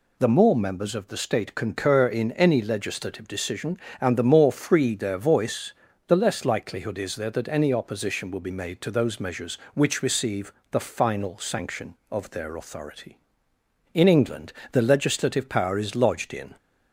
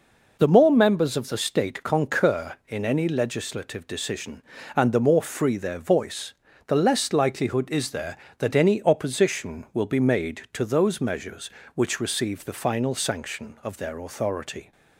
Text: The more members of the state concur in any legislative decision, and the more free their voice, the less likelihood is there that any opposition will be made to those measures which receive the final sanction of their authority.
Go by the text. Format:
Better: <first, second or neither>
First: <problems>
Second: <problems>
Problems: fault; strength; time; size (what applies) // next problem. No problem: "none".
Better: second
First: pauses between "receive" and "the"; slight; at 10.5 s; 0.18 s long // goes on to say "In England the legislative power is lodged in"; strong; from 13.9 s on; 2.6 s long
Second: none